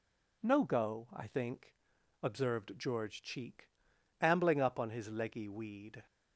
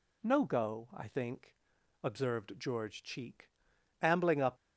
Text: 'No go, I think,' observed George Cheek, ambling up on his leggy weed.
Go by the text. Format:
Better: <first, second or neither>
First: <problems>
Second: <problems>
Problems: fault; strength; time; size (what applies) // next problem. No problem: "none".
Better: first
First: none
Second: stops before "on his leggy weed"; at 4.5 s